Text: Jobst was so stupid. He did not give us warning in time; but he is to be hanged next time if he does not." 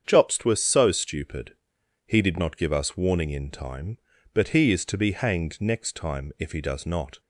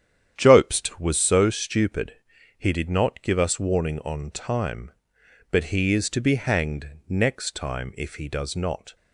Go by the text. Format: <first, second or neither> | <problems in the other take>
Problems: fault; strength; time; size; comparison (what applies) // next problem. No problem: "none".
first | starts louder than the rest; strong; until 1.3 s; 9.5 dB; strong in the first // says "on" for "in"; at 3.9 s // pauses between "hanged" and "next"; slight; at 6.8 s; 0.18 s long